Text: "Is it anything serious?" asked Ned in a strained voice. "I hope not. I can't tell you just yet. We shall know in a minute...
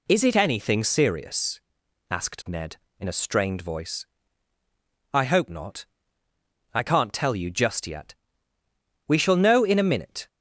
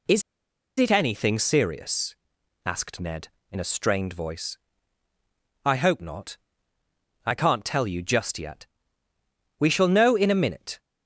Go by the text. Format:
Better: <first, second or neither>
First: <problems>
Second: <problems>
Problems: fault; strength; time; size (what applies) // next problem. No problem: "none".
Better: first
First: none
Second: pauses between "Is" and "it"; noticeable; at 0.2 s; 0.57 s long